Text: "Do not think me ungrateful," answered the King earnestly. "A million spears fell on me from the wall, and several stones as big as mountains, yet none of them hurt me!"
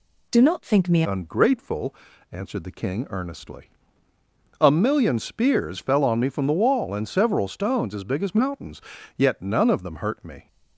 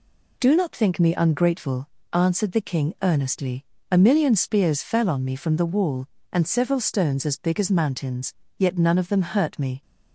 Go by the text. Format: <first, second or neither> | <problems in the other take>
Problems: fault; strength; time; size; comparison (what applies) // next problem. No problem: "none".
second | changes voice at "ungrateful"; from 1.0 s on; 9.4 s long